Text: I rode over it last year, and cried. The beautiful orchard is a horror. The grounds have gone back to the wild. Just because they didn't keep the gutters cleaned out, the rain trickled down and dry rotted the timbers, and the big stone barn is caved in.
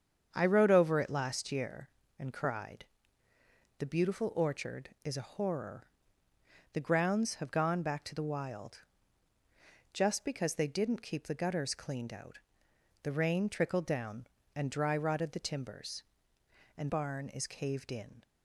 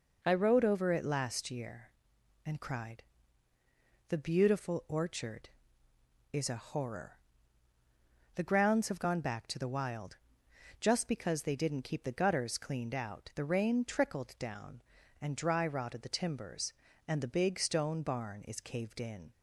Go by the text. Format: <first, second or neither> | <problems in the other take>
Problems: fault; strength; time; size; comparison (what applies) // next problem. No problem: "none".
second | starts louder than the rest; strong; until 1.3 s; 7.5 dB // skips "the big stone"; at 16.8 s